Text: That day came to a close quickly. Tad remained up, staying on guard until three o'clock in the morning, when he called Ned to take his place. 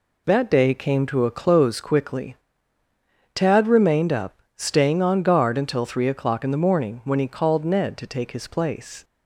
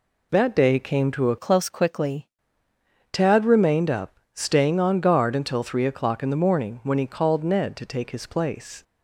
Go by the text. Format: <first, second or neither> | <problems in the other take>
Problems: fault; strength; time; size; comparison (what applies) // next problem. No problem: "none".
first | changes voice from "close" to "quickly"; from 1.3 to 2.2 s; 0.9 s long